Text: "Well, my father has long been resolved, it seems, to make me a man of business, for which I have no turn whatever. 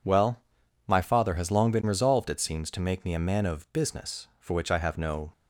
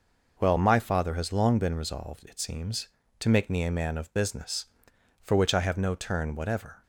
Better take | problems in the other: second | stops before "turn whatever"; at 5.3 s

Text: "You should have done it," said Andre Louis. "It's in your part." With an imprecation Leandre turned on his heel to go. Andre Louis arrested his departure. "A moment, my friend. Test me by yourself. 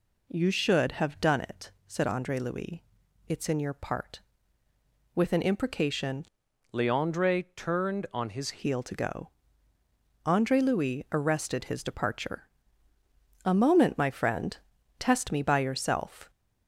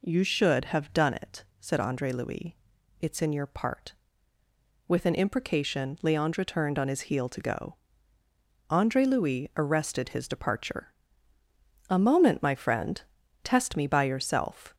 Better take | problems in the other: second | changes voice from "Leandre" to "his"; from 6.7 to 8.5 s; 1.8 s long

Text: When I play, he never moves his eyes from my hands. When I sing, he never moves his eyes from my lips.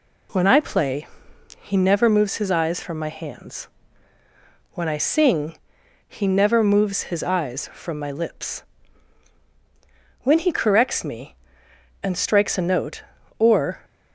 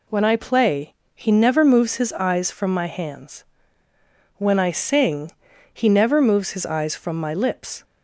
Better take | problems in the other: second | goes on to say "When he corrects me and strikes a note or"; strong; from 10.2 s on; 3.6 s long

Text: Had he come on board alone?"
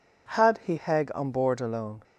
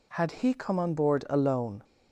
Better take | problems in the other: second | says "heg" for "come"; at 0.7 s

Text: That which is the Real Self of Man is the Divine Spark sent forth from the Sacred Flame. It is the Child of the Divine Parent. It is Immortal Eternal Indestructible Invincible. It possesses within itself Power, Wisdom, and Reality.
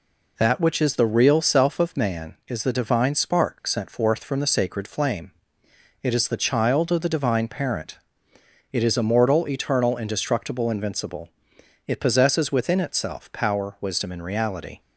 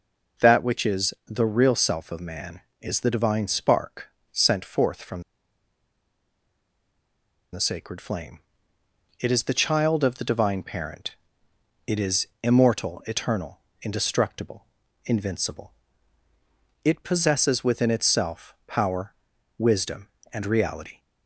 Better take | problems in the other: first | pauses between "Spark" and "sent"; slight; at 4.0 s; 0.22 s long // pauses between "from" and "the"; strong; at 5.2 s; 2.3 s long // pauses between "is" and "Immortal"; slight; at 12.2 s; 0.16 s long // pauses between "Eternal" and "Indestructible"; slight; at 13.5 s; 0.24 s long // pauses between "Indestructible" and "Invincible"; at 14.6 s; 0.40 s long

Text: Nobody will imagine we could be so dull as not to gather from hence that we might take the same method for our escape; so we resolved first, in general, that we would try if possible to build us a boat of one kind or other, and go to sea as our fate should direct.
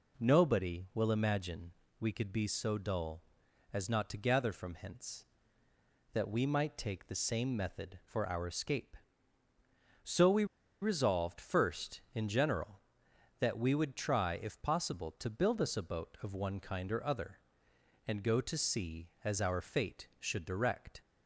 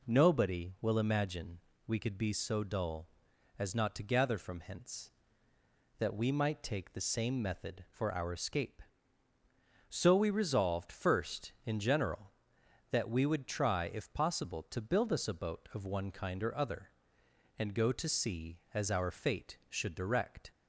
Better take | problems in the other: second | pauses between "imagine" and "we"; slight; at 1.7 s; 0.28 s long; slight in the second // pauses between "we" and "resolved"; at 10.4 s; 0.36 s long

